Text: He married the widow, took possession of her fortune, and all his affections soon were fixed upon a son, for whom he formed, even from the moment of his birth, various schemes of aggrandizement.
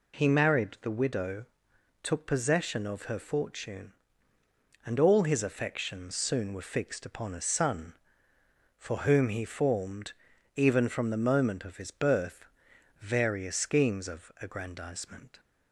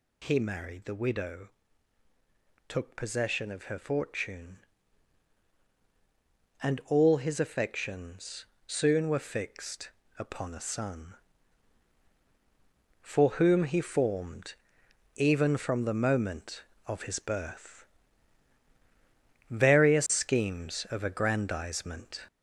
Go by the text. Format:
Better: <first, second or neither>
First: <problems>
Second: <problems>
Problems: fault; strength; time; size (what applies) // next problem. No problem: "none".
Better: first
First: none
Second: gets louder; noticeable; throughout; 4 dB // pauses between "affections" and "soon"; slight; at 8.4 s; 0.20 s long // pauses between "fixed" and "upon"; slight; at 9.8 s; 0.28 s long